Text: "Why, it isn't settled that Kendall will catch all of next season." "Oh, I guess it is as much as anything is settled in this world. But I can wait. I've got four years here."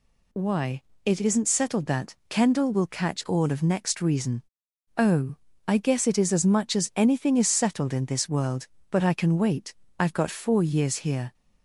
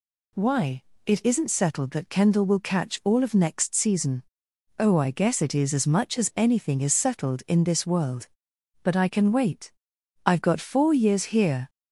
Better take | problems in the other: second | says "reason" for "season"; at 4.0 s

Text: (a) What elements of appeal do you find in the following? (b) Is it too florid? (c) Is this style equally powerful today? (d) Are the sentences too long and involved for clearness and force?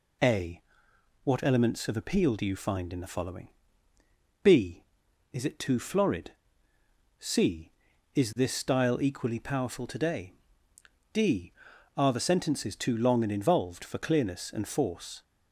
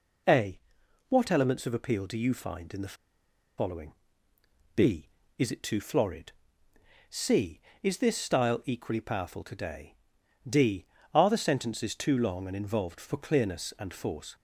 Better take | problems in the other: first | pauses between "the" and "following"; noticeable; at 2.9 s; 0.64 s long

